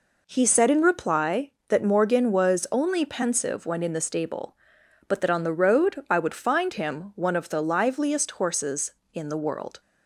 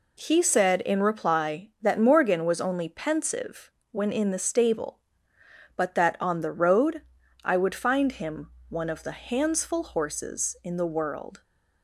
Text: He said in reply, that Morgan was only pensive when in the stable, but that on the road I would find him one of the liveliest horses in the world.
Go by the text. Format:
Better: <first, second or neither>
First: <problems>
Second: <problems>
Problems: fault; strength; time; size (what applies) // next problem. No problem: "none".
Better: first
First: none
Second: pauses between "pensive" and "when"; slight; at 3.7 s; 0.22 s long // pauses between "road" and "I"; at 7.0 s; 0.42 s long // pauses between "him" and "one"; slight; at 8.5 s; 0.18 s long // says "handsful" for "liveliest"; at 9.1 s